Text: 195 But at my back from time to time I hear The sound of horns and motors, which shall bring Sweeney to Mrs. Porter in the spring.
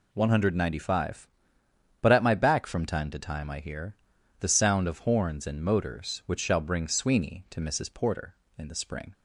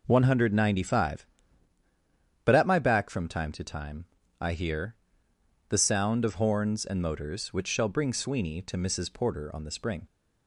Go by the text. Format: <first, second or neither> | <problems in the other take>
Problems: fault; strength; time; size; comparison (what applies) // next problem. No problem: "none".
first | pauses between "time" and "I"; slight; at 4.0 s; 0.34 s long // pauses between "hear" and "The"; noticeable; at 4.9 s; 0.76 s long; also in the first // says "on" for "in"; at 9.5 s